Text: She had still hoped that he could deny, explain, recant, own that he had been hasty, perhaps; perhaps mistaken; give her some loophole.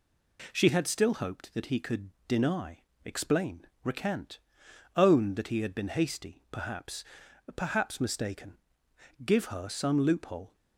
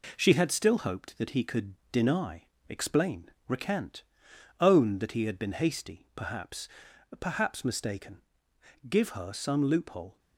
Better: first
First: pauses between "could" and "deny"; slight; at 2.1 s; 0.16 s long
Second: gets quieter; throughout; 3.5 dB // pauses between "could" and "deny"; slight; at 1.7 s; 0.16 s long

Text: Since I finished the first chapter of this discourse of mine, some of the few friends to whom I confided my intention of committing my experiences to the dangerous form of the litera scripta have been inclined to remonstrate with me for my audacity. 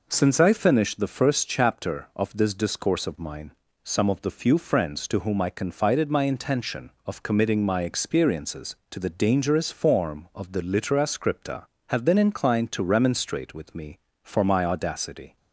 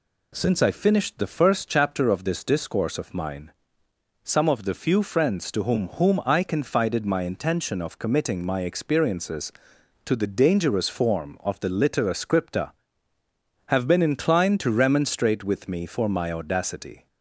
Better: first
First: none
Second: says "whom" twice; at 5.9 s

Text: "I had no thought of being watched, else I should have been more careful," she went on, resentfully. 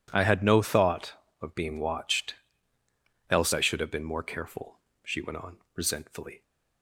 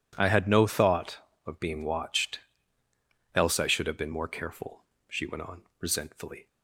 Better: neither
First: none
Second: none

